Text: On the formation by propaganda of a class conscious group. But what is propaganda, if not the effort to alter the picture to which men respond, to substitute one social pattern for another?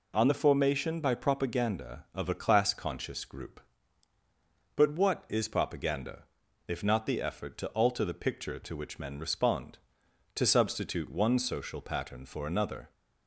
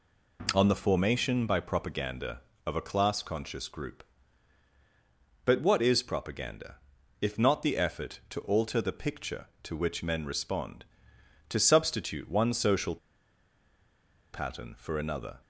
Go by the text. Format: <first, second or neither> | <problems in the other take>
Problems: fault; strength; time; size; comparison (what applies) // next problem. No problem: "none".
first | pauses between "social" and "pattern"; strong; at 12.9 s; 1.3 s long